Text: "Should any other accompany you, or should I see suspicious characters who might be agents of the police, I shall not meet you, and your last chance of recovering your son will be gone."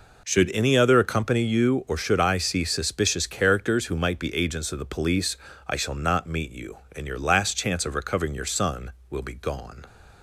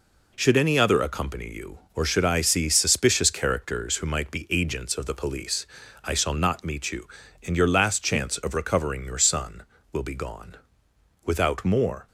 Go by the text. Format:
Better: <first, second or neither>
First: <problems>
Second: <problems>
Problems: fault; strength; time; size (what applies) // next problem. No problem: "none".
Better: first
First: none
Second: goes on to say "Without more"; noticeable; from 11.2 s on; 0.84 s long